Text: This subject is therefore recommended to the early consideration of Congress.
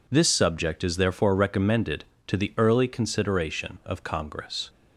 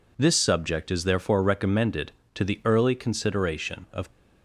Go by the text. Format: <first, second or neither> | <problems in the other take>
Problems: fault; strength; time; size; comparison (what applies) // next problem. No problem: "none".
first | stops before "Congress"; at 4.1 s